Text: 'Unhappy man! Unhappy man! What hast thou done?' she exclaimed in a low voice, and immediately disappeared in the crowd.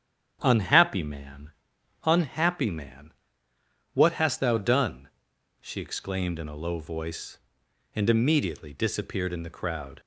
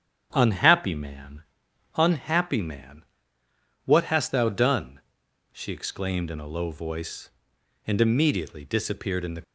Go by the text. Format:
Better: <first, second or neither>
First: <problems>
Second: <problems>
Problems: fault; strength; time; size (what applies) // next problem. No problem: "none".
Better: first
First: starts louder than the rest; strong; until 1.4 s; 9 dB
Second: starts louder than the rest; strong; until 1.3 s; 8.5 dB // stops before "crowd"; at 9.4 s